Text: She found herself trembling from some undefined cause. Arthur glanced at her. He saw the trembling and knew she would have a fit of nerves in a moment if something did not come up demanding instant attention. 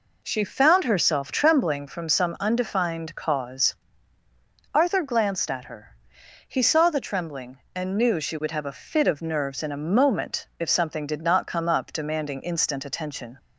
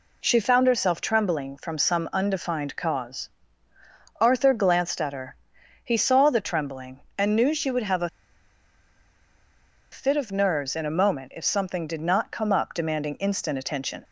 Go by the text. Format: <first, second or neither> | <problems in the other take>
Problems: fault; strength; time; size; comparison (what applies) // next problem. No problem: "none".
first | pauses between "a" and "fit"; strong; at 8.0 s; 1.8 s long